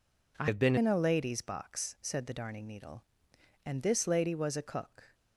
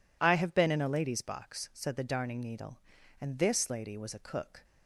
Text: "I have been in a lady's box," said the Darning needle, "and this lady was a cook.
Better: second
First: changes voice from "have" to "been"; from 0.4 to 0.7 s; 0.3 s long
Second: none

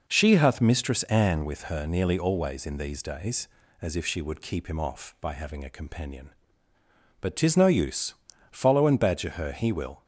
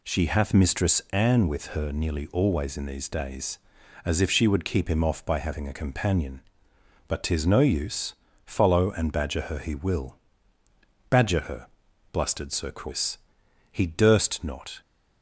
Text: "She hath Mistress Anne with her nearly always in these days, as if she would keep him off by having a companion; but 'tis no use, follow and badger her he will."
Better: first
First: none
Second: goes on to say "Badger her blustered Sir Chris He durst not"; strong; from 11.0 s on; 3.7 s long

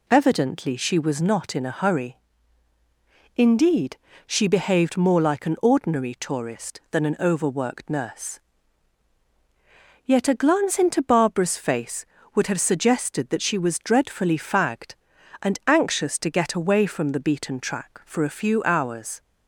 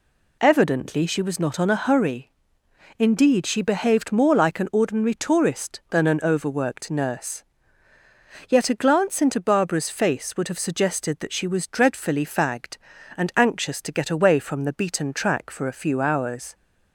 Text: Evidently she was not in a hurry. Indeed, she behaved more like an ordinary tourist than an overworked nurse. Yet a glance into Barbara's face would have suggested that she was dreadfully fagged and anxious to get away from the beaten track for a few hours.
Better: first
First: none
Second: says "on" for "in"; at 1.5 s

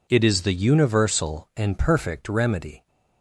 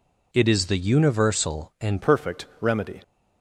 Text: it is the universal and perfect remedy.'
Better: first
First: none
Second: changes voice at "perfect"; from 2.0 s on; 1.0 s long

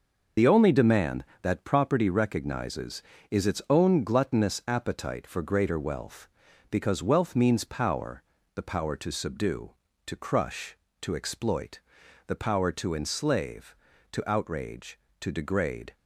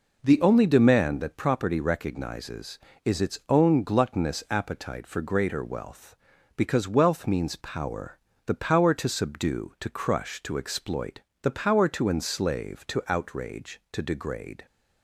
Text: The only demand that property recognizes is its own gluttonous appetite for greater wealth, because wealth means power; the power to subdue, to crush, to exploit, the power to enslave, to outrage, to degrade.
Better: second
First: loses the start of "The"; at 0.3 s; 70 ms // starts louder than the rest; noticeable; until 1.5 s; 6 dB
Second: none

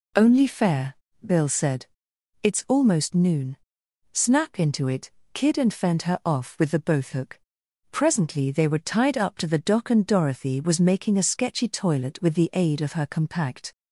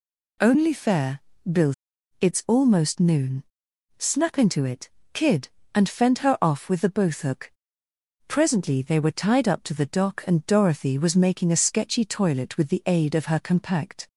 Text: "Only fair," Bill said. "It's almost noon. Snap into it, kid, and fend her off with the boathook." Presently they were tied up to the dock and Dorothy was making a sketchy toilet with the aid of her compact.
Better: first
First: none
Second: skips "said"; at 1.9 s

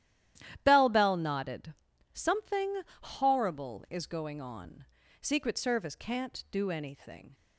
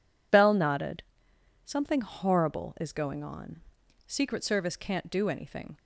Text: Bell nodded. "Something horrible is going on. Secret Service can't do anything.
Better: second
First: starts louder than the rest; strong; until 1.6 s; 12 dB // says "Bell" twice; at 0.9 s // pauses between "Something" and "horrible"; slight; at 2.8 s; 0.20 s long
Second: none

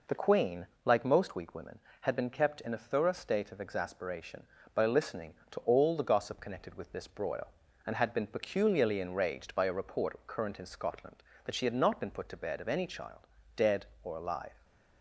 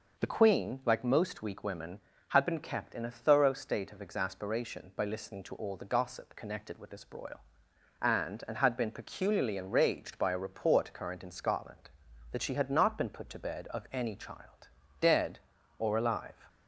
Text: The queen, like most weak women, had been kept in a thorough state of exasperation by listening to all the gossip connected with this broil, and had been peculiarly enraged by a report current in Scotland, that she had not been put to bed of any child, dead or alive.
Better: first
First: none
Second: says "and" twice; at 8.4 s

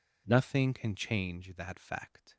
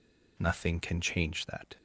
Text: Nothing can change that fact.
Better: first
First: none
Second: stops before "fact"; at 1.7 s

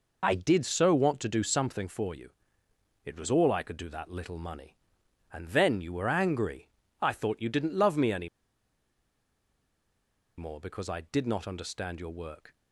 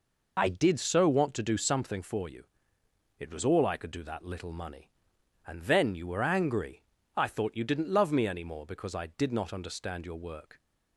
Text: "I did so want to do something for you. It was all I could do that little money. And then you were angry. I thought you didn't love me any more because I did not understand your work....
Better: second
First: pauses between "any" and "more"; strong; at 8.2 s; 2.1 s long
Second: none

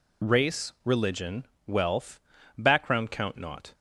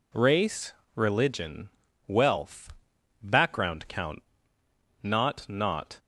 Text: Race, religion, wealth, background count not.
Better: first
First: none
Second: pauses between "count" and "not"; noticeable; at 4.2 s; 0.80 s long // says "not" twice; at 5.4 s

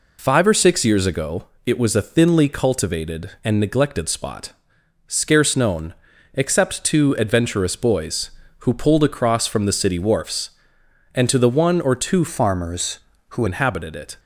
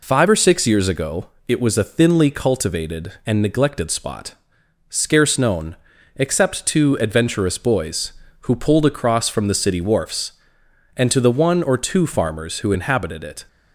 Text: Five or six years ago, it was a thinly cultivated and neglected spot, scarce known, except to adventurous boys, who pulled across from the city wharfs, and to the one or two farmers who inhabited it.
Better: second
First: changes voice from "farmers" to "who"; from 12.2 to 13.4 s; 1.2 s long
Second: none

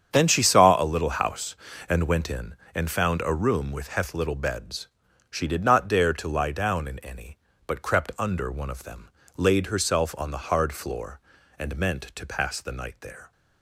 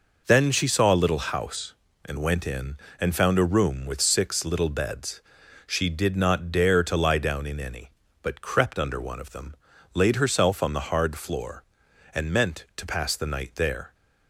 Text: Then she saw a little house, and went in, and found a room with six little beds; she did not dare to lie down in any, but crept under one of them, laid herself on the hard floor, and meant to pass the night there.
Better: second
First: starts louder than the rest; strong; until 1.1 s; 8 dB // says "heth" for "six"; at 3.8 s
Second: none

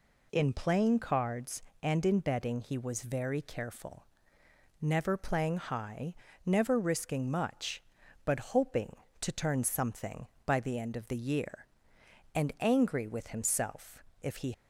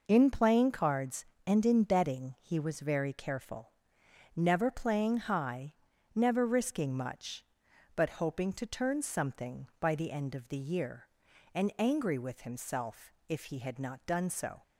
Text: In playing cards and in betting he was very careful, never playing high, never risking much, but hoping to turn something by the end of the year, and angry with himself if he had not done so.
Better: second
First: pauses between "himself" and "if"; slight; at 14.0 s; 0.18 s long // stops before "had not done so"; at 14.5 s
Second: pauses between "himself" and "if"; slight; at 13.1 s; 0.16 s long

